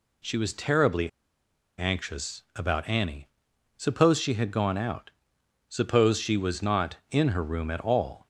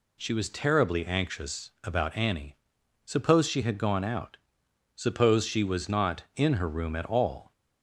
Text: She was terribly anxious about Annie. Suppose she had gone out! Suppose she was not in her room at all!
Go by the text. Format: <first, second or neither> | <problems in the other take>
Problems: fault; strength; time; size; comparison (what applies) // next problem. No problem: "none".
second | pauses between "terribly" and "anxious"; noticeable; at 1.0 s; 0.68 s long